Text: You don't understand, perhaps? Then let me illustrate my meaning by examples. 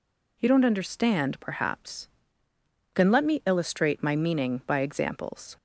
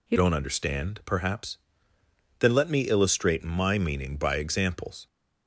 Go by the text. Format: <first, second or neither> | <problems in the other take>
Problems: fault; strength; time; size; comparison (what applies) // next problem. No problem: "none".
first | changes voice at "don't"; from 0.1 s on; 4.9 s long